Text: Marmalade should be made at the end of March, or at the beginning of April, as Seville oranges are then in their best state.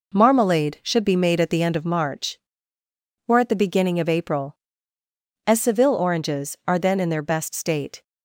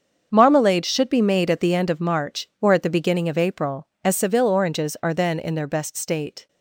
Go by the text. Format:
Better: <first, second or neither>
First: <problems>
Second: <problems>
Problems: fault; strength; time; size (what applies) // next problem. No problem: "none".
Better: first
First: none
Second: gets quieter; strong; throughout; 11.5 dB